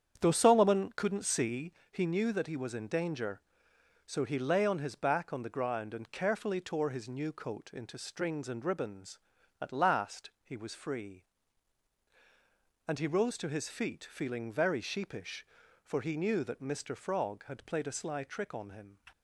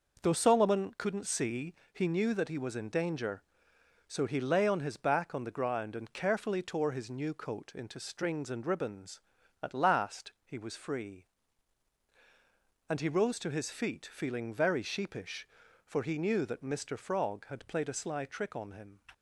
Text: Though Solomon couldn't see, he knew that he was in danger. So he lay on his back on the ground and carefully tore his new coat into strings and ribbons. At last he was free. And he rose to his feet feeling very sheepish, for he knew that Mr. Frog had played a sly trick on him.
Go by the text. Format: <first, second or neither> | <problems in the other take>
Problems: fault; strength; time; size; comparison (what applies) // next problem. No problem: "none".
second | starts louder than the rest; strong; until 1.6 s; 8.5 dB